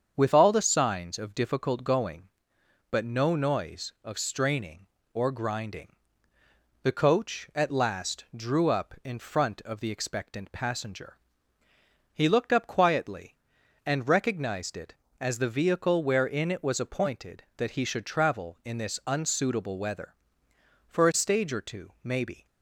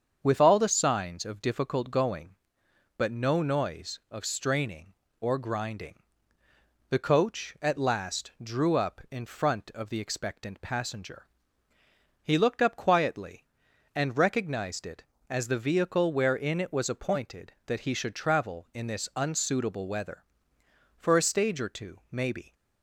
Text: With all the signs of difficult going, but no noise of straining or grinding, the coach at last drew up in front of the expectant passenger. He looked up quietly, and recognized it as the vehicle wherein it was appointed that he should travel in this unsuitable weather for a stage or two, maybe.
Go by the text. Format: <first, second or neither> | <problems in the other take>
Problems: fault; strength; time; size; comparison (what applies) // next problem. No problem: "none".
neither | starts louder than the rest; strong; the same in both